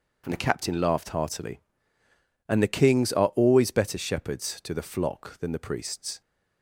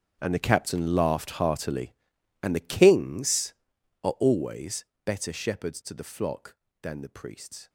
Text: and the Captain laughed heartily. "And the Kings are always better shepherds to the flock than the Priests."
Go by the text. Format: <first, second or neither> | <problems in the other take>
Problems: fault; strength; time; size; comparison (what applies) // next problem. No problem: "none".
first | gets quieter; strong; throughout; 16.5 dB // starts louder than the rest; strong; until 1.2 s; 7.5 dB; also in the first // pauses between "always" and "better"; slight; at 4.8 s; 0.20 s long